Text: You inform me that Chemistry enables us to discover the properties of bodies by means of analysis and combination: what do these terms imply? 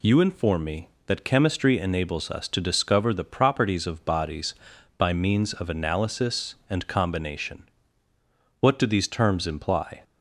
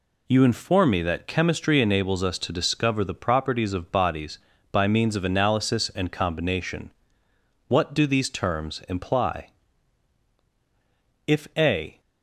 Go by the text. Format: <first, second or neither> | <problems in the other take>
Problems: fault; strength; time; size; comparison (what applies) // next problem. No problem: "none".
first | goes on to say "If a"; noticeable; from 11.2 s on; 0.72 s long